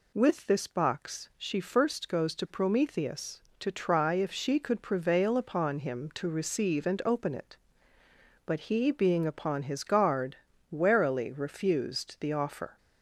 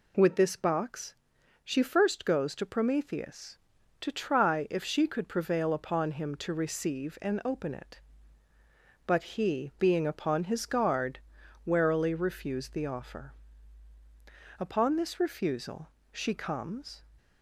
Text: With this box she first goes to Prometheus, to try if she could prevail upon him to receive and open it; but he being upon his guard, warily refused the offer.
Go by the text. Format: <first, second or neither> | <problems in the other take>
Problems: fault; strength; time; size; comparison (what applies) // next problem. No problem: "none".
first | pauses between "box" and "she"; noticeable; at 1.1 s; 0.48 s long // goes on to say "Upon this refusal she comes"; strong; from 14.5 s on; 2.4 s long